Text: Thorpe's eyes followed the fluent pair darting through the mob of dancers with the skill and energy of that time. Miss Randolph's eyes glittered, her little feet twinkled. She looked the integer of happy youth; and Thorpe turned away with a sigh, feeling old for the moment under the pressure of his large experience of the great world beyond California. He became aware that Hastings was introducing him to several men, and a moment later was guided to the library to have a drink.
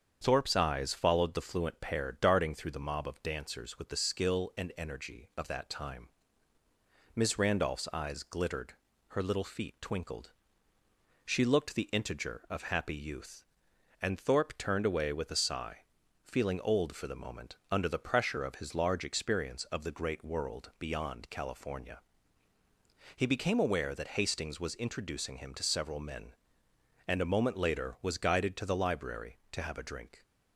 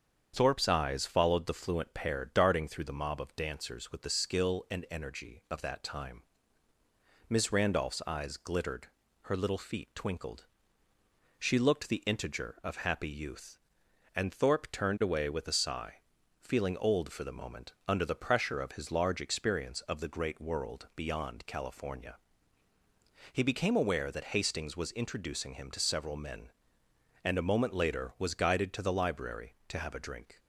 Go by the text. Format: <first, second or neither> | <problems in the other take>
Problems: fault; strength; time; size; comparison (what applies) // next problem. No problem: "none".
neither | starts louder than the rest; strong; the same in both // pauses between "moment" and "under"; slight; the same in both